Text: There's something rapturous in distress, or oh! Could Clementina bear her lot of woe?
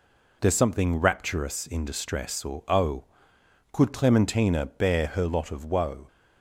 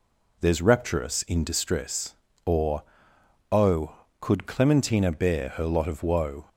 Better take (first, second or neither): first